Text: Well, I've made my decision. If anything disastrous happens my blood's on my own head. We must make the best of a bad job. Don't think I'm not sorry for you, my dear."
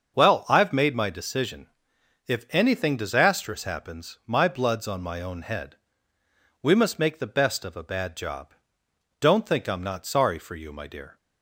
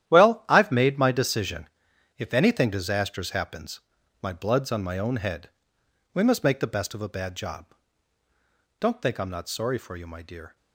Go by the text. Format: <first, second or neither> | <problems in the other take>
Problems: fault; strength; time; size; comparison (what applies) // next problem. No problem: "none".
first | gets quieter; strong; throughout; 11.5 dB // starts louder than the rest; strong; until 1.1 s; 11.5 dB; also in the first // pauses between "happens" and "my"; at 3.7 s; 0.42 s long